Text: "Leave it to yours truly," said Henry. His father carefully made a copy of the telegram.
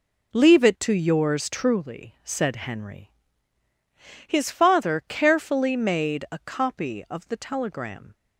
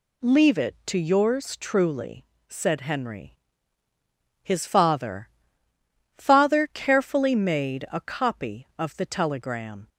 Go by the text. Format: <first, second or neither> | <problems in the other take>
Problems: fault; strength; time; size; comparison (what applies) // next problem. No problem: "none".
first | says "father" twice; at 6.1 s